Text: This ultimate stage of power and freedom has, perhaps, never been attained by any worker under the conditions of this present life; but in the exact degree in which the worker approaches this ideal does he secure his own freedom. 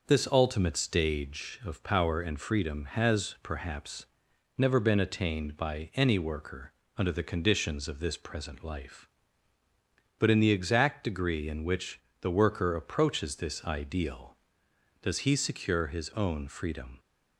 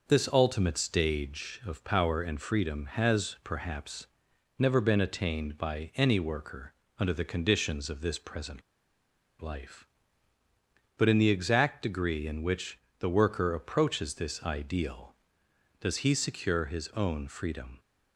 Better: first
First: pauses between "worker" and "under"; slight; at 6.7 s; 0.21 s long // pauses between "which" and "the"; slight; at 12.0 s; 0.20 s long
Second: pauses between "worker" and "under"; slight; at 6.7 s; 0.22 s long // pauses between "present" and "life"; noticeable; at 8.6 s; 0.79 s long // pauses between "which" and "the"; slight; at 12.7 s; 0.20 s long

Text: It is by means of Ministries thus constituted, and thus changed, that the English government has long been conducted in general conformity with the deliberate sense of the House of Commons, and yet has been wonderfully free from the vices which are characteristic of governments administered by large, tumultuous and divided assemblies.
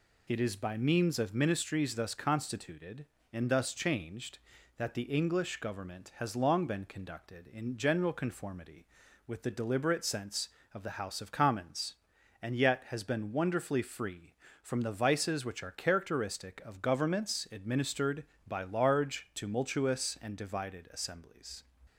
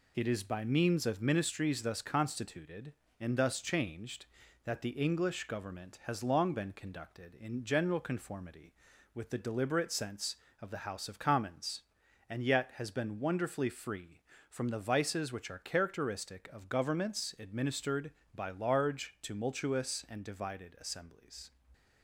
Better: first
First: none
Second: gets quieter; noticeable; throughout; 4.5 dB

